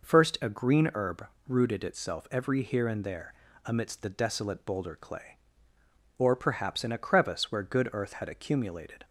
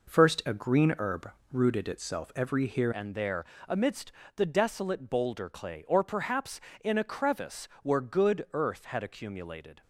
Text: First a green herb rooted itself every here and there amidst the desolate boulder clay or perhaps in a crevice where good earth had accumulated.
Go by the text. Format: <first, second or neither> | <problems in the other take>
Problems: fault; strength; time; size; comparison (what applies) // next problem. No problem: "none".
first | pauses between "herb" and "rooted"; slight; at 1.3 s; 0.22 s long; slight in the first // changes voice at "and"; from 2.9 s on; 6.9 s long // pauses between "there" and "amidst"; slight; at 3.4 s; 0.22 s long; slight in the first // pauses between "amidst" and "the"; slight; at 4.1 s; 0.24 s long // pauses between "crevice" and "where"; slight; at 7.6 s; 0.16 s long